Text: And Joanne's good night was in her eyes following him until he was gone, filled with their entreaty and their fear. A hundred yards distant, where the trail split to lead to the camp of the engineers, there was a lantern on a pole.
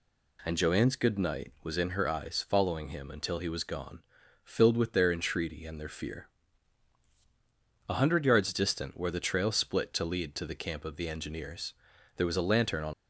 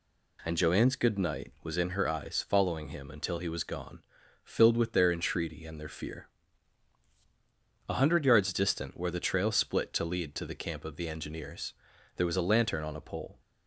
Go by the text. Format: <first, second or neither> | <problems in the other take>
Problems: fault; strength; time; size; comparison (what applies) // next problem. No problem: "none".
second | stops before "a pole"; at 12.9 s